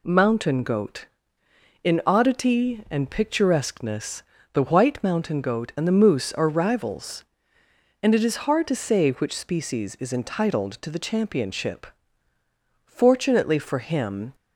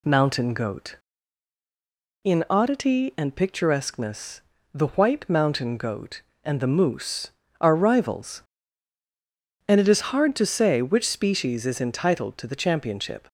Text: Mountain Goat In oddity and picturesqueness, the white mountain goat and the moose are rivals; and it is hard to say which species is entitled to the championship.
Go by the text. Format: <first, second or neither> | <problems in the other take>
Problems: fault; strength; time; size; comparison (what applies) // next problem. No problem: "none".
second | goes on to say "Fortunately for him"; from 12.8 s on; 1.5 s long